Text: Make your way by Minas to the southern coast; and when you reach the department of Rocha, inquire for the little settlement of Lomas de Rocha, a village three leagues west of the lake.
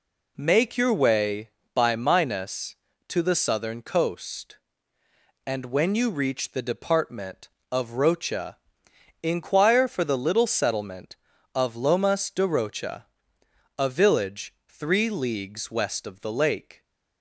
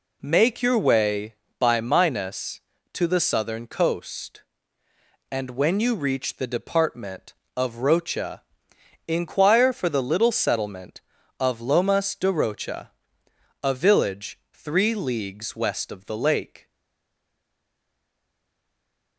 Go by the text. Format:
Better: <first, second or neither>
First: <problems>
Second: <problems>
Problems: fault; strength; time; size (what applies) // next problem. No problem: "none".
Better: first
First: none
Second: stays silent after the last word; strong; from 16.6 s on; 2.5 s long